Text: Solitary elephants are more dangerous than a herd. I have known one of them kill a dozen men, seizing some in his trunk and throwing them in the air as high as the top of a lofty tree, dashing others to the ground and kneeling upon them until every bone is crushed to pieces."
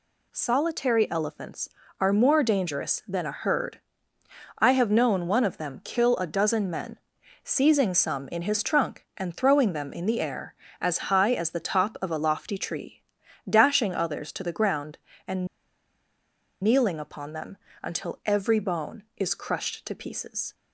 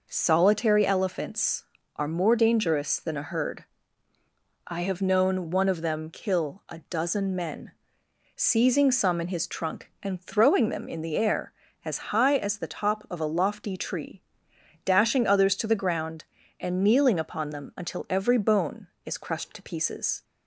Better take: second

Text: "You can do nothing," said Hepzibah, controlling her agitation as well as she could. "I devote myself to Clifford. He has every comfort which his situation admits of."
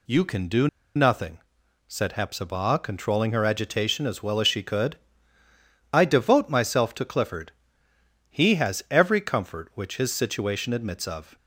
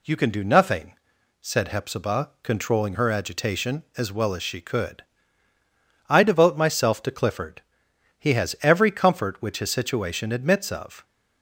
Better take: second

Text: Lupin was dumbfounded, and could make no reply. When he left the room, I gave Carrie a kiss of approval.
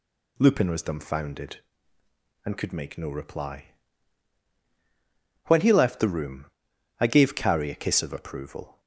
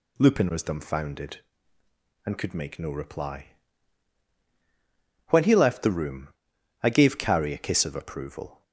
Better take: neither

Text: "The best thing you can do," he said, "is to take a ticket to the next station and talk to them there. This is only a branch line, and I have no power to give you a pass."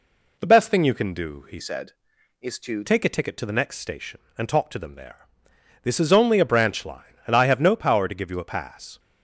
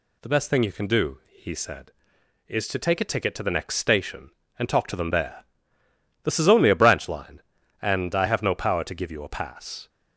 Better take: second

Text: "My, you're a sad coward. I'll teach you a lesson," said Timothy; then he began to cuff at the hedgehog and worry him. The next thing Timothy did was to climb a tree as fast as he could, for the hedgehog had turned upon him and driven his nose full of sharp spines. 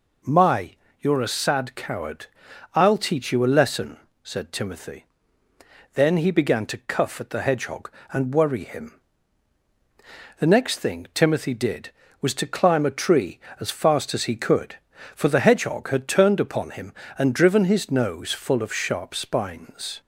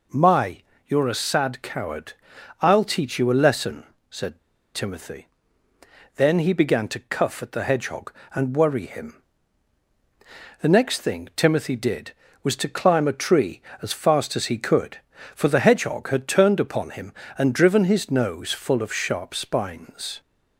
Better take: first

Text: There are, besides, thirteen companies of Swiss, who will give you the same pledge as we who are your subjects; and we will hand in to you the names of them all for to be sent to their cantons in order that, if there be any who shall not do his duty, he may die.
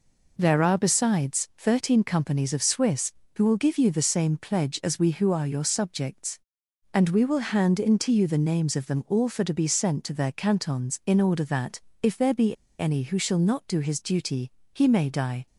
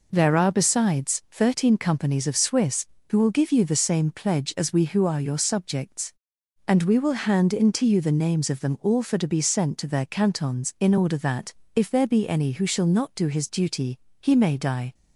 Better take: second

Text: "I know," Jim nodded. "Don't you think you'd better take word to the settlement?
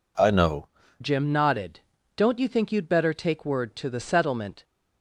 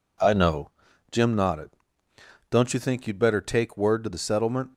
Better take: second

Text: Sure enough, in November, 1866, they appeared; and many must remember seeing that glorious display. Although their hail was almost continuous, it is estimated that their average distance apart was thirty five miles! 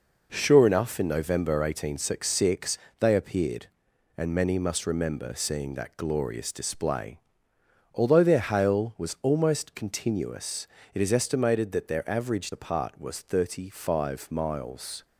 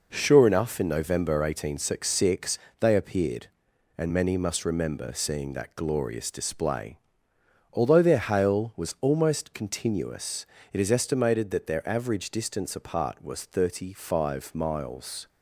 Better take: second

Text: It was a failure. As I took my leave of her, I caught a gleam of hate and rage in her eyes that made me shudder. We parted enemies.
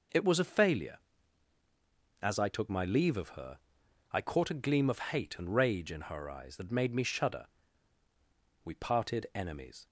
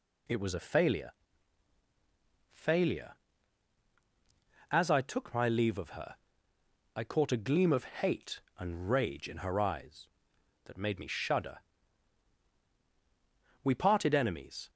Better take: first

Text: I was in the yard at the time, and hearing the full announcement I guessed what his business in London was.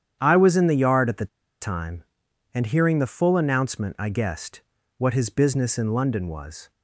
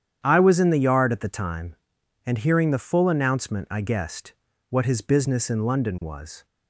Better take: second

